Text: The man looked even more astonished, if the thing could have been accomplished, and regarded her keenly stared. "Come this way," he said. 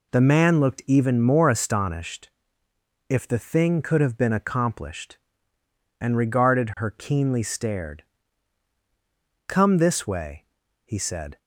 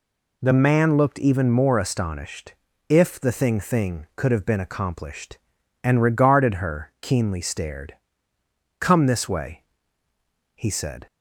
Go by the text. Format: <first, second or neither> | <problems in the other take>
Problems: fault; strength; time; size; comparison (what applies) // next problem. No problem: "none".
first | says "thing" twice; at 3.6 s